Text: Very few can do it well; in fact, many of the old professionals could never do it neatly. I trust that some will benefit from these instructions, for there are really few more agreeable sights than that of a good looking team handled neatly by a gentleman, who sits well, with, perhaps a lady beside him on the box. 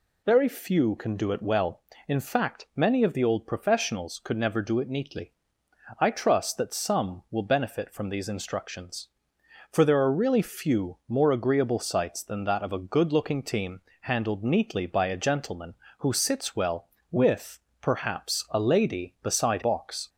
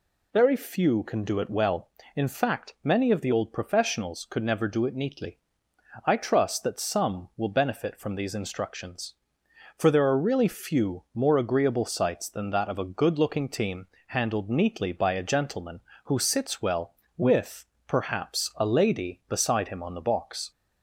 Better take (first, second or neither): second